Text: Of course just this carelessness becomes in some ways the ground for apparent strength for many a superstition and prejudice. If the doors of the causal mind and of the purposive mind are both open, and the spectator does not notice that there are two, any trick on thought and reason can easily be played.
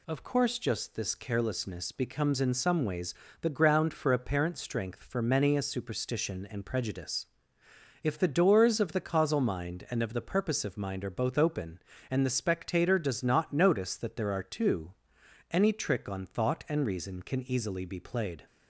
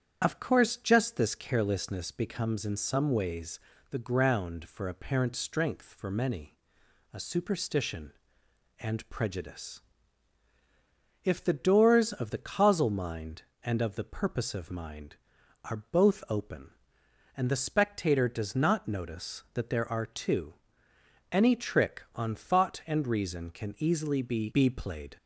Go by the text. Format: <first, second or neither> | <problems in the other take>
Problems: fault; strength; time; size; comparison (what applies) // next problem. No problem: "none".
first | starts louder than the rest; strong; until 1.2 s; 8 dB // pauses between "ways" and "the"; slight; at 3.5 s; 0.32 s long; slight in the first // pauses between "many" and "a"; noticeable; at 6.5 s; 0.58 s long // says "be" twice; at 24.5 s